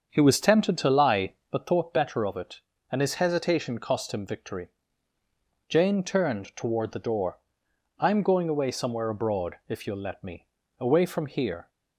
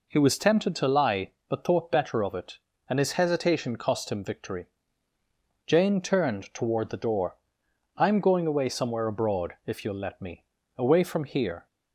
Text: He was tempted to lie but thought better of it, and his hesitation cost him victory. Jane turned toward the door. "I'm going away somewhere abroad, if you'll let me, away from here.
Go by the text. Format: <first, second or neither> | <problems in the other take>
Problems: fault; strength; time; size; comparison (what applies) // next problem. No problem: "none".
second | starts louder than the rest; until 1.6 s; 7 dB